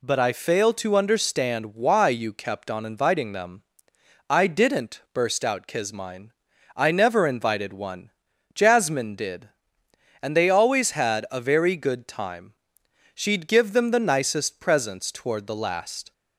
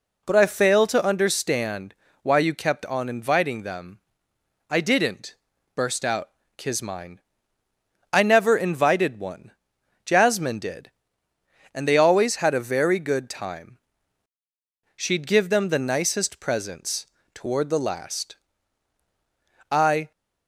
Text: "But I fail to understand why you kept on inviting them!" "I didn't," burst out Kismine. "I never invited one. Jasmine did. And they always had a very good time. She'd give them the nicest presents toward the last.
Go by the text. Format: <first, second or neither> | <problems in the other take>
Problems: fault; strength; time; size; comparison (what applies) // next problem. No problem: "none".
first | pauses between "understand" and "why"; slight; at 1.9 s; 0.28 s long // pauses between "out" and "Kismine"; slight; at 6.2 s; 0.30 s long // pauses between "presents" and "toward"; slight; at 17.0 s; 0.32 s long // goes on to say "I"; slight; from 19.7 s on; 0.40 s long